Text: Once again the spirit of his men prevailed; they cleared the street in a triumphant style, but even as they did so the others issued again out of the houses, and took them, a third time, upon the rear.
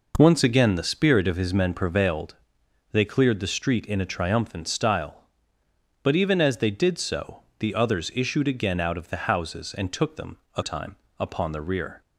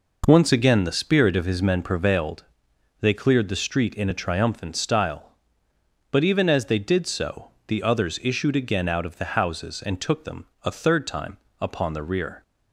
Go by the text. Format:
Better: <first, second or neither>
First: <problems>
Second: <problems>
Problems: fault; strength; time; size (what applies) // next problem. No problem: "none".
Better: second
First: pauses between "so" and "the"; slight; at 7.4 s; 0.16 s long // skips "third"; at 10.6 s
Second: pauses between "so" and "the"; slight; at 7.5 s; 0.16 s long